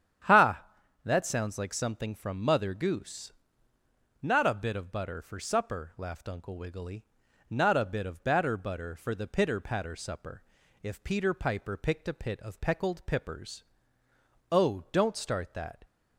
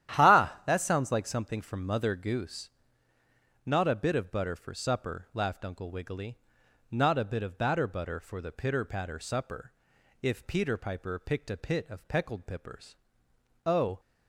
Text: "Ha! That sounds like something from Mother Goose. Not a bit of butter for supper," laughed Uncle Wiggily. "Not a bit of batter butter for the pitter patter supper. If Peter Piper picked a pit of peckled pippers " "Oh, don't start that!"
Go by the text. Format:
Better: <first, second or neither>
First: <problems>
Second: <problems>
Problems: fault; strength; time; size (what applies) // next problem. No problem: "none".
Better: first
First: starts louder than the rest; strong; until 1.6 s; 9.5 dB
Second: starts louder than the rest; strong; until 1.2 s; 11.5 dB // stops before "don't start that"; at 13.9 s